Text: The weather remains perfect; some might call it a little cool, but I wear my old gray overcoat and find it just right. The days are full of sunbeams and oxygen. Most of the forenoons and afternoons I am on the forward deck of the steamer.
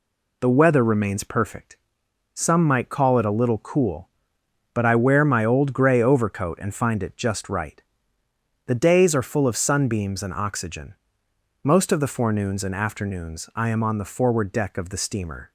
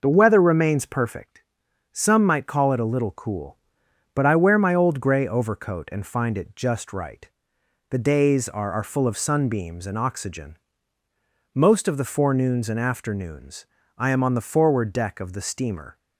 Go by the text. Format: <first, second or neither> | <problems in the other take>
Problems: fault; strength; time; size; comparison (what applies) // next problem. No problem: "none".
first | says "are" twice; at 8.7 s // pauses between "afternoons" and "I"; slight; at 13.6 s; 0.32 s long